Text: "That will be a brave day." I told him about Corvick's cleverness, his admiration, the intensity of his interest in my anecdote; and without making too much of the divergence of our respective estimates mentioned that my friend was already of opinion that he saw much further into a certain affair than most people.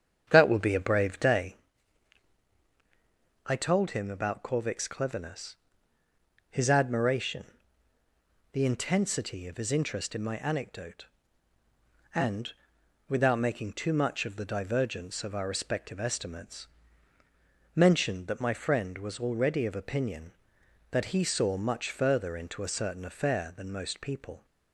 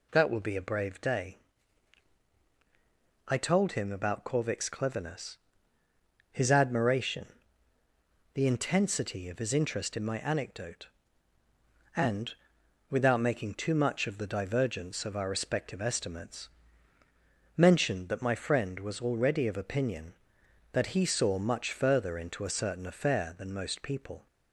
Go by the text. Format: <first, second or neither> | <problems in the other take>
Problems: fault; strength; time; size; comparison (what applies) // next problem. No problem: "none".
second | starts louder than the rest; strong; until 1.7 s; 8 dB // pauses between "and" and "without"; noticeable; at 12.5 s; 0.54 s long; noticeable in the second // pauses between "estimates" and "mentioned"; at 16.6 s; 1.1 s long; also in the second